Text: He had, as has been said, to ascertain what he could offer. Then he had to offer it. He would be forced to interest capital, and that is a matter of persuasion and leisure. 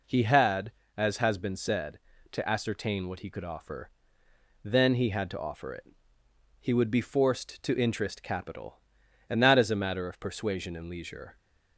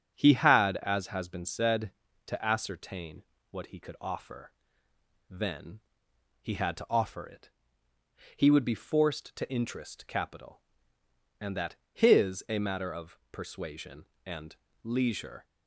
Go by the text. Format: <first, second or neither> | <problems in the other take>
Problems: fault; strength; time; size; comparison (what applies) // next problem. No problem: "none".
first | starts louder than the rest; strong; until 1.1 s; 7.5 dB // pauses between "ascertain" and "what"; slight; at 3.2 s; 0.28 s long // pauses between "Then" and "he"; noticeable; at 5.8 s; 0.61 s long // says "his" for "is"; at 11.9 s // pauses between "and" and "leisure"; slight; at 14.5 s; 0.26 s long